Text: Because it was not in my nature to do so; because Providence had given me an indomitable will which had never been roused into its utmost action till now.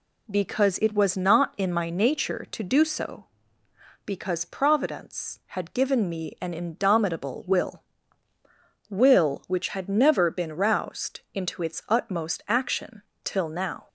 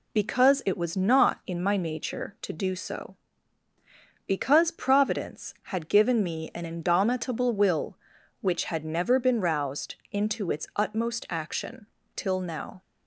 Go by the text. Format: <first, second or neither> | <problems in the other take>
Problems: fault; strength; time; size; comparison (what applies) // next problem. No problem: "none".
second | says "will" twice; at 8.8 s // pauses between "action" and "till"; slight; at 13.0 s; 0.22 s long; slight in the second